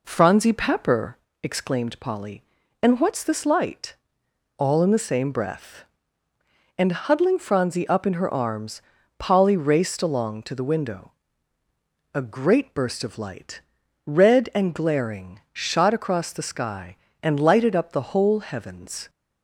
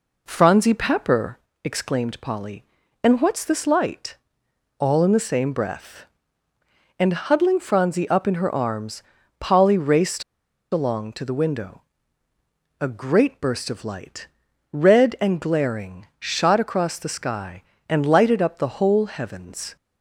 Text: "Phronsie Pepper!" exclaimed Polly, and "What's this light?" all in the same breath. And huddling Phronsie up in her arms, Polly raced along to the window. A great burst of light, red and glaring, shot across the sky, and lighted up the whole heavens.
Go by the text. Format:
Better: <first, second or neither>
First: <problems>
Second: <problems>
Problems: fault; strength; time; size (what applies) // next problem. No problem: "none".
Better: first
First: none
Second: pauses between "raced" and "along"; noticeable; at 10.2 s; 0.50 s long